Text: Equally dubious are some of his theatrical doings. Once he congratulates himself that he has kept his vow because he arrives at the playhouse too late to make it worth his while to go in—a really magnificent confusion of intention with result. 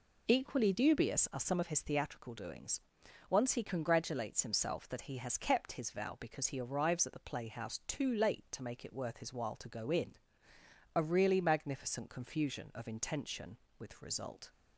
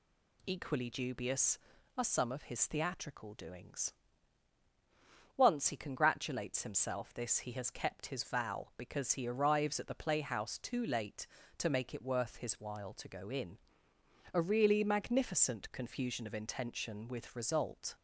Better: first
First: none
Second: says "this" for "that"; at 7.1 s

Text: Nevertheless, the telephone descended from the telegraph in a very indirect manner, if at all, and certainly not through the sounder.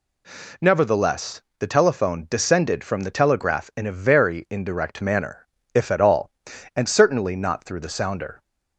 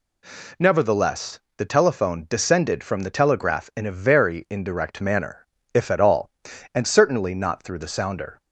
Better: neither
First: none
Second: none

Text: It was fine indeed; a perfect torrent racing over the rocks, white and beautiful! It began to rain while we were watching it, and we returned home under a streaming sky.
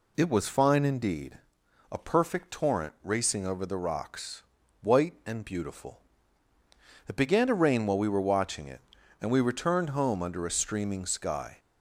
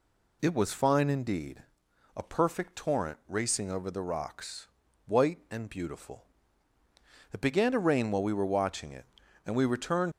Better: first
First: none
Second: stops before "home under a streaming sky"; at 10.1 s

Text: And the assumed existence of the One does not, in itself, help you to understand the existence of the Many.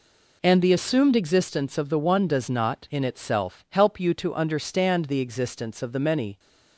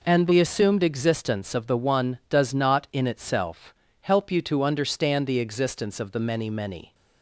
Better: first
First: none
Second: says "Many" twice; at 6.5 s

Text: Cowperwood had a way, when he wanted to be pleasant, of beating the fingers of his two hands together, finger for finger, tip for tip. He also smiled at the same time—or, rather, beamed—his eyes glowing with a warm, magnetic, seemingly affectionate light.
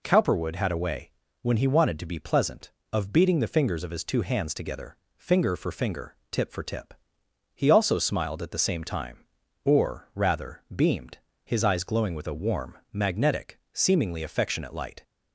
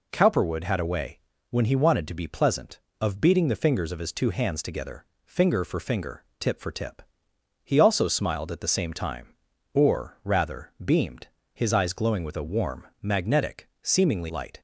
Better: first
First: none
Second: skips "affectionate"; at 14.3 s

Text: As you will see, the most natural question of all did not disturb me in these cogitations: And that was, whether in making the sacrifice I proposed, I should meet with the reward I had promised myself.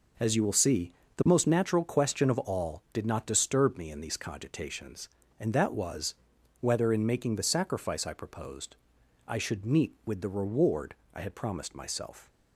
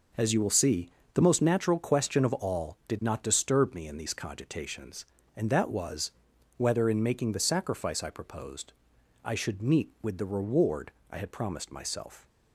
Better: neither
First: pauses between "reward" and "I"; slight; at 10.9 s; 0.18 s long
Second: pauses between "reward" and "I"; slight; at 10.9 s; 0.18 s long

